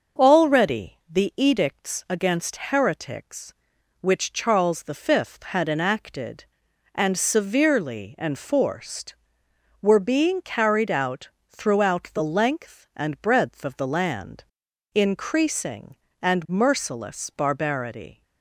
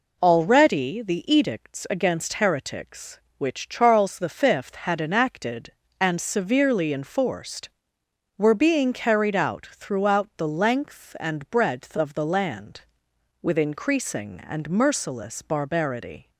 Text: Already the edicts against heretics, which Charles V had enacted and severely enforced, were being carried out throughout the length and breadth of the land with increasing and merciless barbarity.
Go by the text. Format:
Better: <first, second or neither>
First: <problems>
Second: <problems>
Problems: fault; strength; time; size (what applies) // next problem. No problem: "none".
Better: second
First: pauses between "out" and "throughout"; slight; at 11.2 s; 0.22 s long // skips "with"; at 14.6 s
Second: none